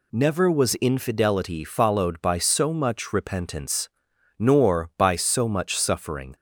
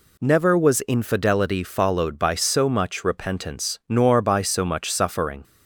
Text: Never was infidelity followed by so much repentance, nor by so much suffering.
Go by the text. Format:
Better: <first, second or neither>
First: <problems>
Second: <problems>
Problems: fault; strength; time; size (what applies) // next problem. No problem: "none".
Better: neither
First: none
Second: none